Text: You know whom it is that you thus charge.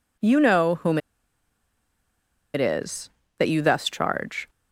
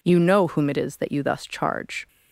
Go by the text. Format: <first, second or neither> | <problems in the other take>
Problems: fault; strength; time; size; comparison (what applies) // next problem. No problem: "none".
second | pauses between "whom" and "it"; strong; at 0.9 s; 1.5 s long